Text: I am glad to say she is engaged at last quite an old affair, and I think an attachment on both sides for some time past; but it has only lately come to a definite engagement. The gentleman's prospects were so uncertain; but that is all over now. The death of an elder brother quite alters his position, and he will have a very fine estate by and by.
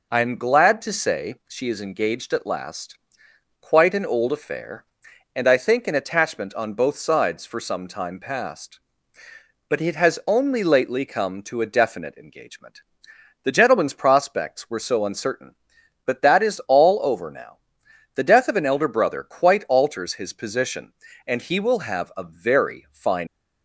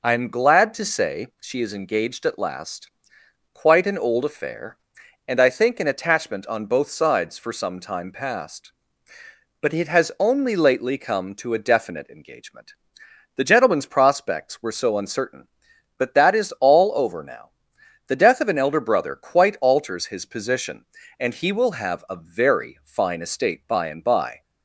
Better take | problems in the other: second | pauses between "last" and "quite"; noticeable; at 2.9 s; 0.64 s long; noticeable in the second // stops before "estate by and by"; at 23.2 s

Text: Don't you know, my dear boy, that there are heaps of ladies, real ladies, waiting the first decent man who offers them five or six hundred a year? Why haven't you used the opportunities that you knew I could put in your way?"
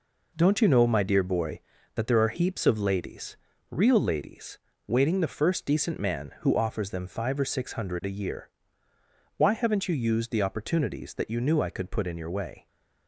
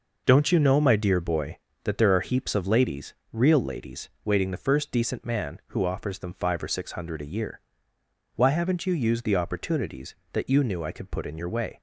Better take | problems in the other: neither | none

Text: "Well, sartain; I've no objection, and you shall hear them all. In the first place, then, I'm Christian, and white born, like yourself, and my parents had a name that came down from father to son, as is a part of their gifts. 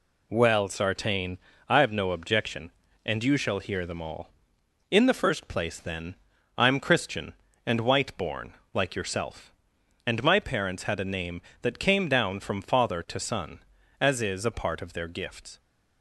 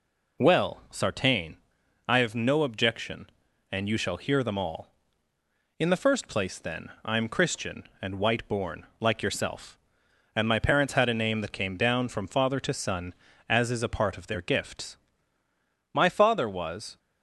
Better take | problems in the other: first | goes on to say "My father was"; noticeable; from 15.9 s on; 1.0 s long

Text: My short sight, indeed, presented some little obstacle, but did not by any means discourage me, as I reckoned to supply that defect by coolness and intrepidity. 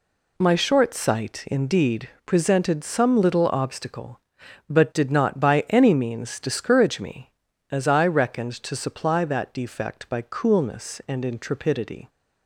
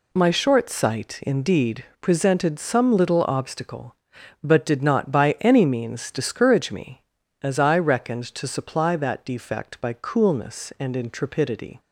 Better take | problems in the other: neither | none

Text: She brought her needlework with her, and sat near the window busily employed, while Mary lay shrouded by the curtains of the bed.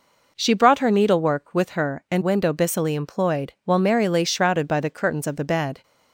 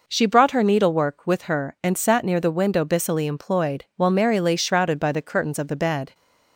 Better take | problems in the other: second | skips "sat near the"; at 2.2 s

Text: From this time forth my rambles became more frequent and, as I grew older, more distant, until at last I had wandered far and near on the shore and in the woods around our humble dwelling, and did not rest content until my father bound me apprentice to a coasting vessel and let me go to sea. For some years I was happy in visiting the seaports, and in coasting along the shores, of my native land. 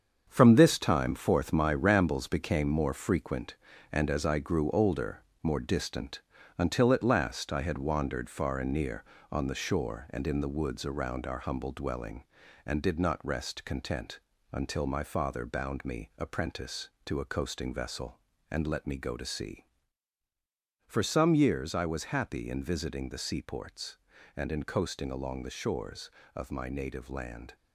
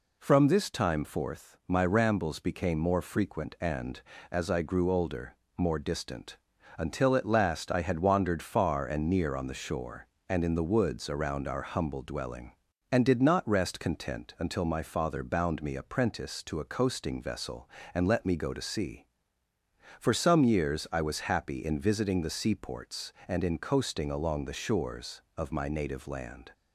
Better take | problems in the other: second | gets quieter; strong; throughout; 8 dB // pauses between "content" and "until"; slight; at 14.1 s; 0.32 s long

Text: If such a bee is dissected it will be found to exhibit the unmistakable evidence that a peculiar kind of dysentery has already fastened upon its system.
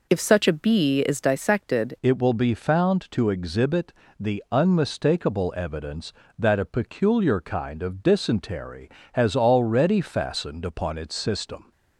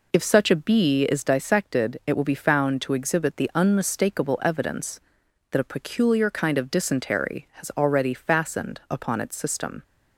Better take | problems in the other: second | changes voice at "it"; from 2.0 s on; 9.7 s long // pauses between "exhibit" and "the"; slight; at 3.9 s; 0.26 s long

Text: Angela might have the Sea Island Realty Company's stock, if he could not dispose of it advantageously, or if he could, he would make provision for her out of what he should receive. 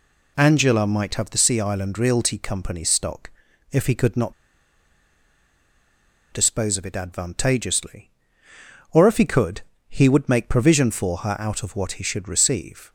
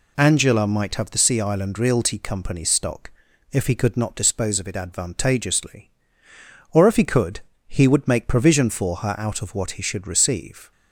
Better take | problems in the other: second | pauses between "not" and "dispose"; strong; at 4.3 s; 1.9 s long

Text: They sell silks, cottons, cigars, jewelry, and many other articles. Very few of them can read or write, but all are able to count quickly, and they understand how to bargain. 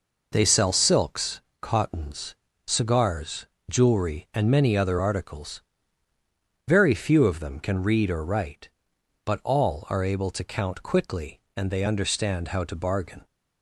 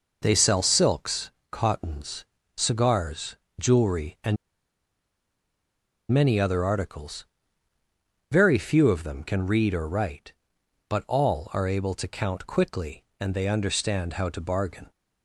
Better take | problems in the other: first | pauses between "and" and "many"; strong; at 4.3 s; 1.7 s long

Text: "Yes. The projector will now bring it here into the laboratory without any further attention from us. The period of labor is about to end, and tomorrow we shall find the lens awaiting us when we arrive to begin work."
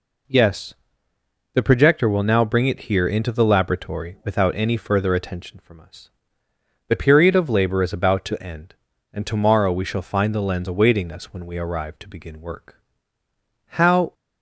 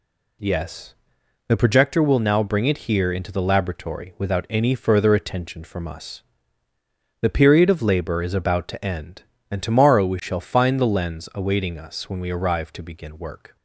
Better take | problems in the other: second | goes on to say "How"; slight; from 13.6 s on; 0.48 s long

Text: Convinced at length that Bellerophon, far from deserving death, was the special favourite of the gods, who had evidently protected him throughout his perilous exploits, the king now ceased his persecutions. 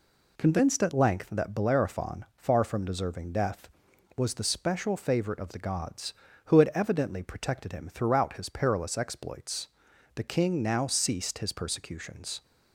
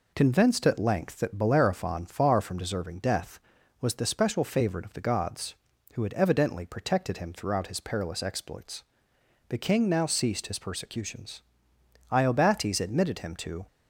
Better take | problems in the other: first | goes on to say "Iobates admitted him to"; from 12.0 s on; 1.5 s long

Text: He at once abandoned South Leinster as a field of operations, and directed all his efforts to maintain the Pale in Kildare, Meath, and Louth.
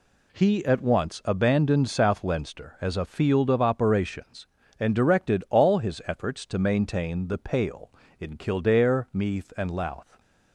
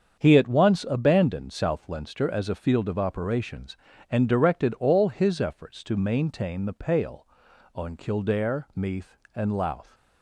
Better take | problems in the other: first | starts louder than the rest; strong; until 1.2 s; 7.5 dB // says "on" for "in"; at 7.7 s

